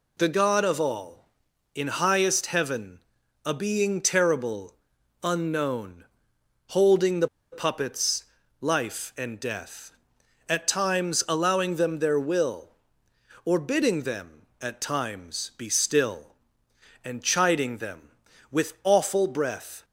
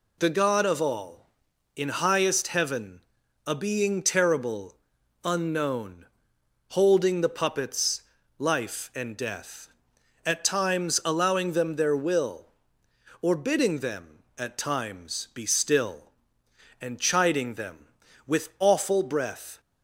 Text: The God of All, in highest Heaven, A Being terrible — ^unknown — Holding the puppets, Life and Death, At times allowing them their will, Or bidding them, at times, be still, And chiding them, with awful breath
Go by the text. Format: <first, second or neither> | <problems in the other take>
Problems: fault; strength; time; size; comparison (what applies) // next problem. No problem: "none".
second | pauses between "the" and "puppets"; slight; at 7.2 s; 0.25 s long